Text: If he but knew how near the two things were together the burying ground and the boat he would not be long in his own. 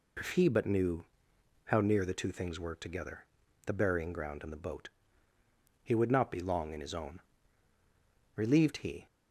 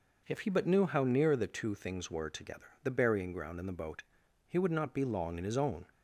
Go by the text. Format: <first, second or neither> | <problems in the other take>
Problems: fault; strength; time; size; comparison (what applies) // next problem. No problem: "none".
second | pauses between "knew" and "how"; noticeable; at 1.0 s; 0.62 s long // pauses between "together" and "the"; at 3.2 s; 0.42 s long // pauses between "boat" and "he"; noticeable; at 4.8 s; 0.94 s long; also in the second // goes on to say "Relieved he"; noticeable; from 8.3 s on; 0.70 s long